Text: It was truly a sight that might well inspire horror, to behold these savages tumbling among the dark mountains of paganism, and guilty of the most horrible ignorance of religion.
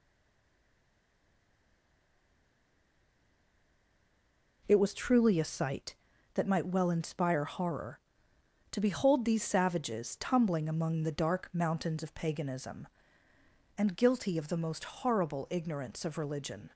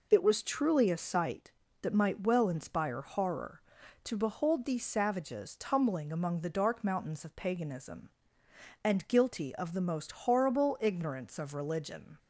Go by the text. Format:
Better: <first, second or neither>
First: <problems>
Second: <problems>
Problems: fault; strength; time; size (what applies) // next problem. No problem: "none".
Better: second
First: stays silent before the first word; strong; until 4.6 s; 4.6 s long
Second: none